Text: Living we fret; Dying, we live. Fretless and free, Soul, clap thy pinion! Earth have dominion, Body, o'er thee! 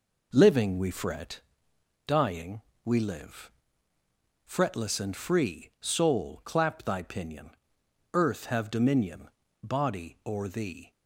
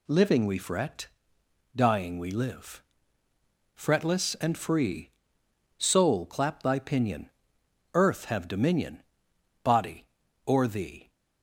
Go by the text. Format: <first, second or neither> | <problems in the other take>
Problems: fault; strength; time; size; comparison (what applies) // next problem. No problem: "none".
neither | none